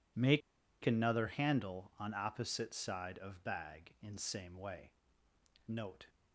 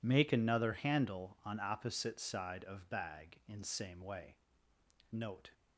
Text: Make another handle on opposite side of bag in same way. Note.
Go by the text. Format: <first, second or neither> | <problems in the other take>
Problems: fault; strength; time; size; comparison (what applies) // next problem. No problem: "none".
second | pauses between "Make" and "another"; at 0.4 s; 0.44 s long